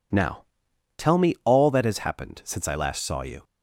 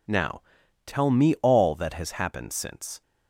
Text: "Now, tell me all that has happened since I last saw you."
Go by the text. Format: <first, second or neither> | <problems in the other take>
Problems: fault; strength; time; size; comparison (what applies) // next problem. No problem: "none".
first | stops before "I last saw you"; at 3.0 s